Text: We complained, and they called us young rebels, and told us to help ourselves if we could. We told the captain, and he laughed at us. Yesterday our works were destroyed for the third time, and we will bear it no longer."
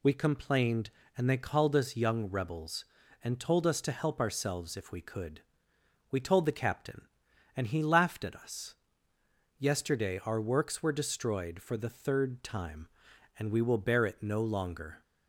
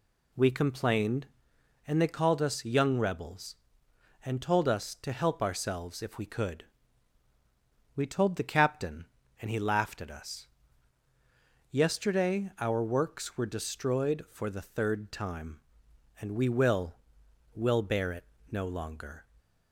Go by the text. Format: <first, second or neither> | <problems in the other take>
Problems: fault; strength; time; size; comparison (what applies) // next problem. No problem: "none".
first | says "will" twice; at 17.5 s // pauses between "it" and "no"; slight; at 18.2 s; 0.26 s long